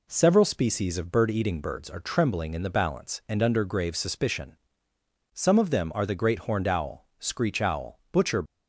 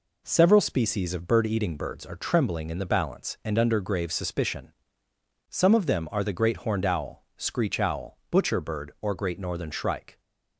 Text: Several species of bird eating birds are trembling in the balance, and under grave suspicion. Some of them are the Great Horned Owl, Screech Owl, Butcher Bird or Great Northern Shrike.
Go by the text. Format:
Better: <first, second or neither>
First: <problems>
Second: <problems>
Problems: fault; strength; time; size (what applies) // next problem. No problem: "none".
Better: second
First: stops before "Bird or Great Northern Shrike"; at 8.4 s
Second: none